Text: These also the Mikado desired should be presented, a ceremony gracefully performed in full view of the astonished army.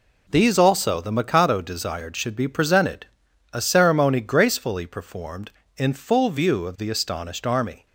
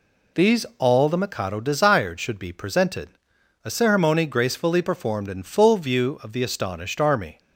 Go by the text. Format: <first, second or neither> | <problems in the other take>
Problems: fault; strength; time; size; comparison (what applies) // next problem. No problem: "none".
first | says "all" for "also"; at 0.7 s